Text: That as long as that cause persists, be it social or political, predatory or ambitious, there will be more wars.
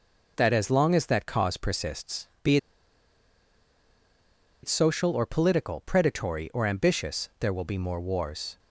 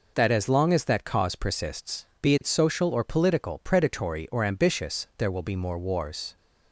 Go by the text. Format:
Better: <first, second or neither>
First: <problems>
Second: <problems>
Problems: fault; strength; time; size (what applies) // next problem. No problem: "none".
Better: second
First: pauses between "be" and "it"; strong; at 2.5 s; 2.0 s long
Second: none